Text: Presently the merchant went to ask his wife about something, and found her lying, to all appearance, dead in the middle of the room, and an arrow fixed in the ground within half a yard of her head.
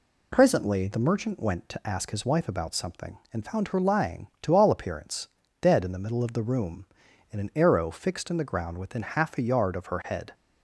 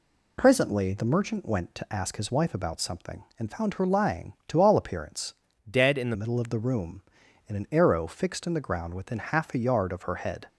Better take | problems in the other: first | changes voice from "dead" to "the"; from 5.6 to 6.1 s; 0.5 s long

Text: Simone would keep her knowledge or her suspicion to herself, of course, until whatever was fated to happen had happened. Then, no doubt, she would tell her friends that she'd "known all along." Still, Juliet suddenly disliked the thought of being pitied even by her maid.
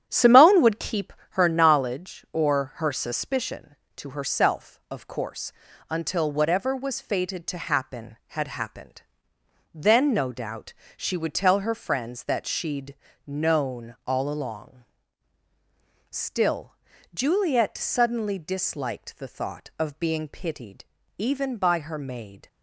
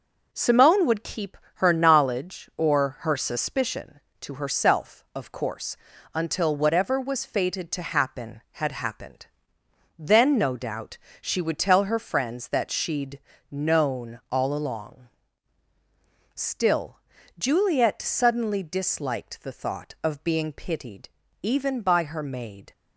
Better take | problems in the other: second | starts louder than the rest; strong; until 1.5 s; 9.5 dB // pauses between "keep" and "her"; slight; at 1.1 s; 0.20 s long; slight in the second // pauses between "she'd" and "known"; slight; at 12.9 s; 0.30 s long; slight in the second // pauses between "pitied" and "even"; slight; at 20.8 s; 0.32 s long; slight in the second

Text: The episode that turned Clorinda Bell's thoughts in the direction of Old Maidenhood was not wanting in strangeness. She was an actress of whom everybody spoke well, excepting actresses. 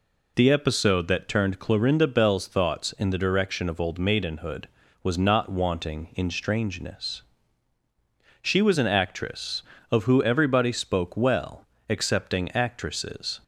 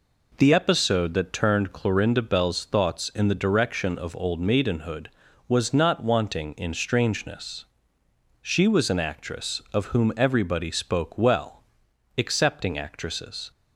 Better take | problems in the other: second | says "who" for "whom"; at 10.0 s

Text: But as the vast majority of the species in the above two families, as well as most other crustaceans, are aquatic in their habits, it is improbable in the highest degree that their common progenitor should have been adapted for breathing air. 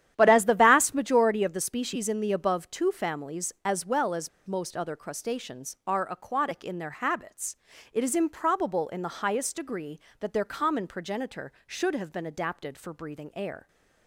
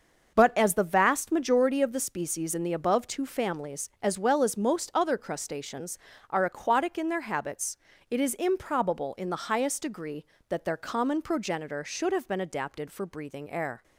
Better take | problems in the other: second | starts louder than the rest; strong; until 1.1 s; 11 dB; also in the second // pauses between "as" and "most"; slight; at 4.2 s; 0.18 s long

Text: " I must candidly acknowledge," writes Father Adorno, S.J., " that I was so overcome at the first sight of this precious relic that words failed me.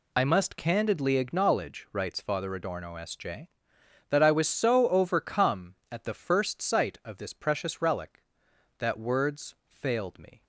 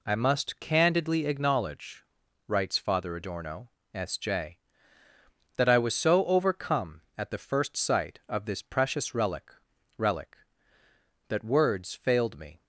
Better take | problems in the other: first | says "relic" twice; at 9.9 s

